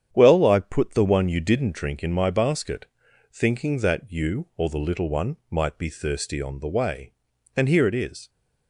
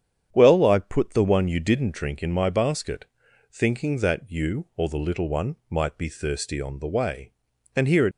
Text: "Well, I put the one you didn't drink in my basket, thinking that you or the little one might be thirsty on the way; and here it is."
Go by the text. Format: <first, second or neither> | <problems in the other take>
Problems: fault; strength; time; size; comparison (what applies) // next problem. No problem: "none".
first | starts louder than the rest; strong; until 1.3 s; 8.5 dB; strong in the first // stops before "is"; at 8.1 s